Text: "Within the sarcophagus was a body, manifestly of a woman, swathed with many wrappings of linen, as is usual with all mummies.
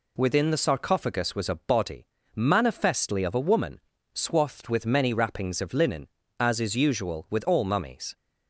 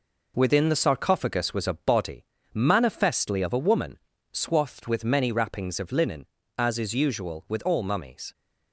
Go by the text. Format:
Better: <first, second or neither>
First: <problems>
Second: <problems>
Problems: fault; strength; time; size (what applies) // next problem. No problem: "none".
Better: first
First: none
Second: gets quieter; noticeable; throughout; 5.5 dB